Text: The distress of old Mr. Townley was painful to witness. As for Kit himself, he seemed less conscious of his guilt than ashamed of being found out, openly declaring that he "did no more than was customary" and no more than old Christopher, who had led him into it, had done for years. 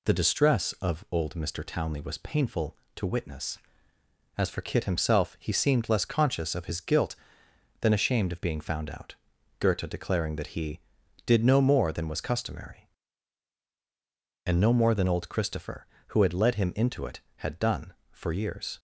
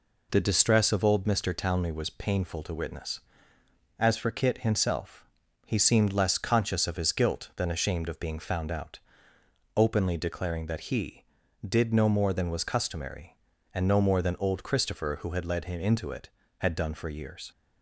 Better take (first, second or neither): second